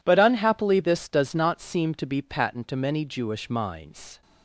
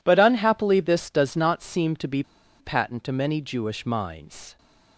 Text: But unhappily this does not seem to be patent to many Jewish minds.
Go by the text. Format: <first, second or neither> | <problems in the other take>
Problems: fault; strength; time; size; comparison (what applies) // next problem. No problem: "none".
first | pauses between "be" and "patent"; at 2.2 s; 0.36 s long